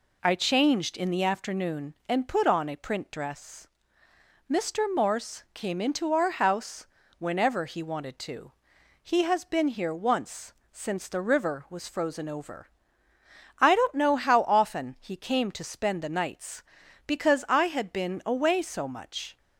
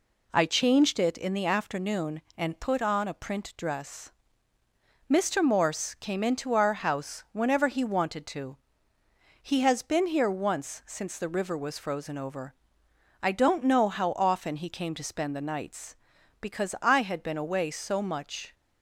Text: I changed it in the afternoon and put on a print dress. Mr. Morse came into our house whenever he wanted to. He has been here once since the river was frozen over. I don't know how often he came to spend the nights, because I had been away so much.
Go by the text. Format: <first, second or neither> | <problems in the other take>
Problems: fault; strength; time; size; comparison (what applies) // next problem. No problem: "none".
second | skips "it"; at 0.9 s // pauses between "house" and "whenever"; slight; at 6.8 s; 0.34 s long // pauses between "once" and "since"; slight; at 10.5 s; 0.22 s long